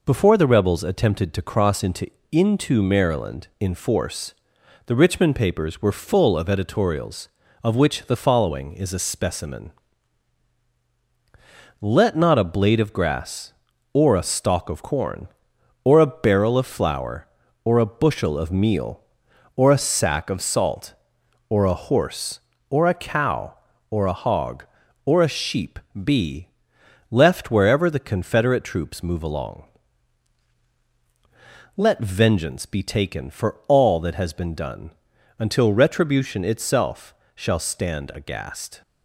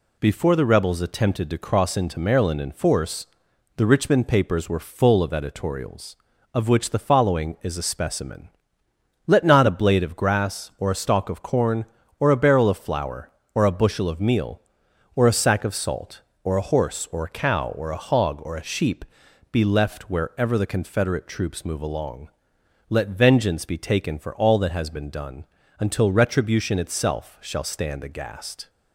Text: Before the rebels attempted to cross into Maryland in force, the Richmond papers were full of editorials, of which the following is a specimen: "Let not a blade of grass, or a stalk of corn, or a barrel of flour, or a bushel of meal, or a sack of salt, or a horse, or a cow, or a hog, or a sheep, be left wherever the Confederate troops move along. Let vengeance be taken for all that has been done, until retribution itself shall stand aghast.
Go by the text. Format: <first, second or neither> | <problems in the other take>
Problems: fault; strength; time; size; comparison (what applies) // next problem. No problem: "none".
second | says "into" twice; at 2.3 s // pauses between "be" and "left"; noticeable; at 26.4 s; 0.64 s long // pauses between "itself" and "shall"; slight; at 37.1 s; 0.20 s long